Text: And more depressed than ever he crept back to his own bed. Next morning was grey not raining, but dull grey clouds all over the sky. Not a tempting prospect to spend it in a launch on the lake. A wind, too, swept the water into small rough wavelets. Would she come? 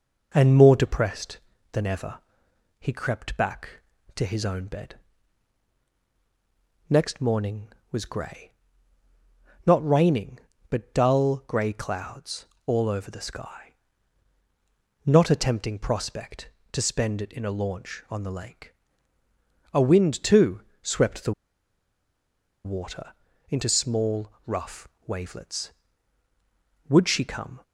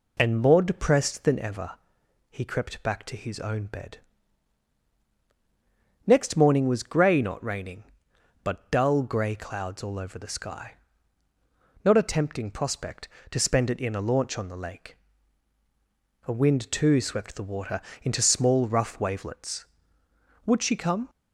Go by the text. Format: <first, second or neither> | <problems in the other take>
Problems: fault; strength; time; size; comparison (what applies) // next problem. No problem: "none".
second | pauses between "ever" and "he"; noticeable; at 2.1 s; 0.60 s long; noticeable in the second // pauses between "grey" and "not"; at 8.4 s; 1.1 s long // pauses between "clouds" and "all"; slight; at 12.4 s; 0.20 s long // pauses between "the" and "water"; strong; at 21.3 s; 1.3 s long // pauses between "water" and "into"; slight; at 23.1 s; 0.36 s long; slight in the second // pauses between "rough" and "wavelets"; slight; at 24.8 s; 0.20 s long